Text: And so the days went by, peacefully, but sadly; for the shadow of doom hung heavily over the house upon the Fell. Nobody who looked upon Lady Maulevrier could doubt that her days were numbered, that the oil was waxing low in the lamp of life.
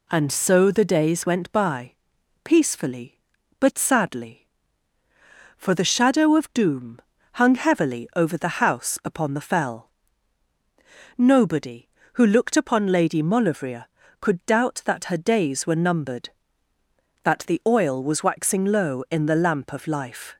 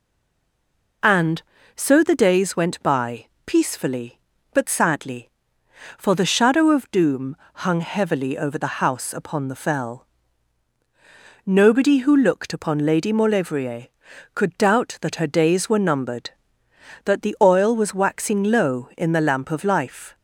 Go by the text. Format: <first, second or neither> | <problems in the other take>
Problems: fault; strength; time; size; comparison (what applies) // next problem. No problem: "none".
first | stays silent before the first word; until 1.0 s; 1.0 s long // pauses between "doom" and "hung"; slight; at 7.3 s; 0.26 s long; slight in the first